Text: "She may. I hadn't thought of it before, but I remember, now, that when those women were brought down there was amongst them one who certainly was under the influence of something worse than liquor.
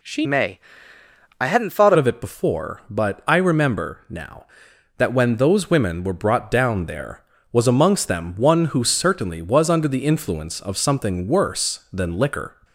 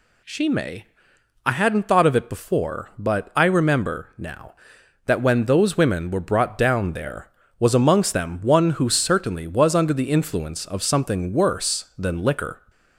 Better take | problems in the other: second | changes voice from "may" to "thought"; from 0.2 to 1.9 s; 1.7 s long

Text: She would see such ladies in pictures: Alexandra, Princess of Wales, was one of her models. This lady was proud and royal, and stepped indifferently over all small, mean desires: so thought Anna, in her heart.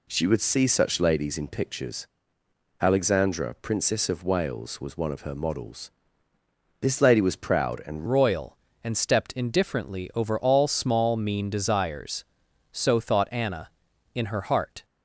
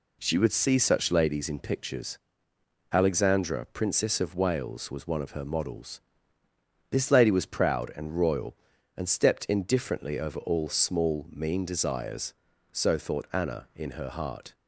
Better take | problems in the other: second | changes voice at "royal"; from 8.0 s on; 6.8 s long

